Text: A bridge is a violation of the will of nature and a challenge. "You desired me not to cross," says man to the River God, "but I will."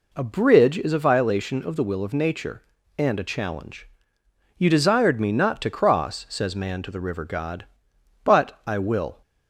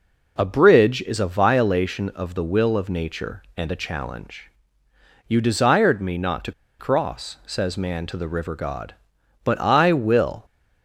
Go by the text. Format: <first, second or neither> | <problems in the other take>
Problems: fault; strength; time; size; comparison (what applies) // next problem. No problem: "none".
first | pauses between "to" and "cross"; slight; at 6.5 s; 0.28 s long